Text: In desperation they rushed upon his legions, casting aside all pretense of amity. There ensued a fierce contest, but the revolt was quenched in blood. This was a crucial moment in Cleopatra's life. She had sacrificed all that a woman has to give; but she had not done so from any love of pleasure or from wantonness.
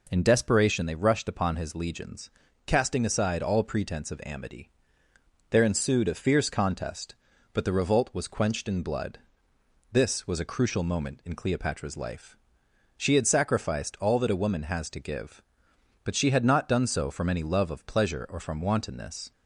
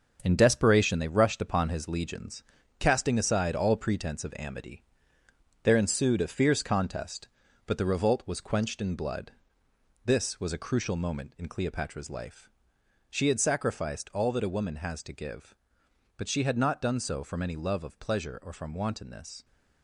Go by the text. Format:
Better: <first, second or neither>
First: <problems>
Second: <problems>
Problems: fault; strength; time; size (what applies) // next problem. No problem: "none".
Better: first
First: none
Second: gets quieter; strong; throughout; 7.5 dB